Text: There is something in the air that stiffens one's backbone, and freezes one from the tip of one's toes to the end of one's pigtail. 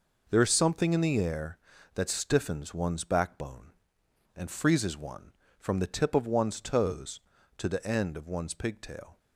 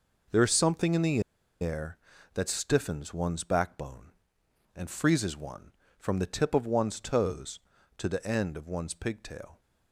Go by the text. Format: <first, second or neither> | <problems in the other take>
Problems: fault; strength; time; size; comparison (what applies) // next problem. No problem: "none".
first | pauses between "the" and "air"; at 1.1 s; 0.41 s long